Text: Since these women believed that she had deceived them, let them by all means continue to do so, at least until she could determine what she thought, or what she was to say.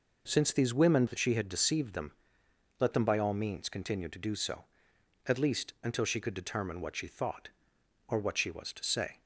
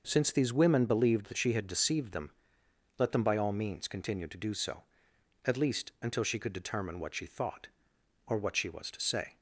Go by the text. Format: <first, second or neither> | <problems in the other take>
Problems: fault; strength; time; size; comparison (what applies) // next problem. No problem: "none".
second | skips "believed"; at 1.0 s